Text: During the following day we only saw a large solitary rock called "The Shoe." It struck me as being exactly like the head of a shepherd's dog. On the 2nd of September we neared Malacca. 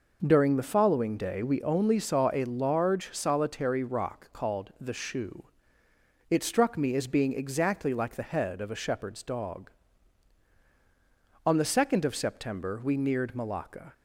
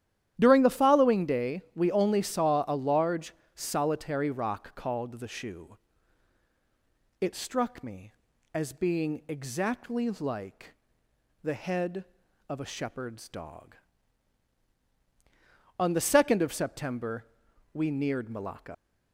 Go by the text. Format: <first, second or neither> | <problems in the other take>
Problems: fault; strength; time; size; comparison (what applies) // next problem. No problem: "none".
first | starts louder than the rest; strong; until 1.4 s; 11.5 dB // pauses between "large" and "solitary"; slight; at 3.3 s; 0.22 s long // pauses between "like" and "the"; noticeable; at 10.7 s; 0.70 s long // pauses between "September" and "we"; noticeable; at 17.2 s; 0.48 s long // leaves "Malacca" unfinished; at 18.7 s; 80 ms